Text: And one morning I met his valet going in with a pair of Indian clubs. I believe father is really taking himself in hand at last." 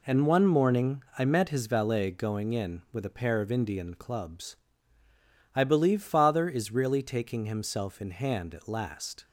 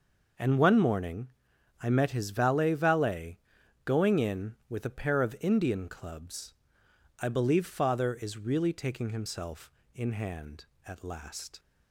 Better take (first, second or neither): first